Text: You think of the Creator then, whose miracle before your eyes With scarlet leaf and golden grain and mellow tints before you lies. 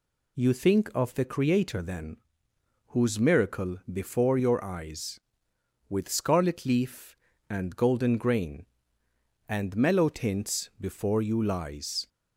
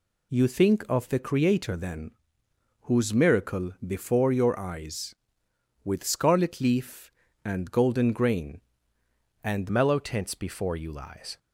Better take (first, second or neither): first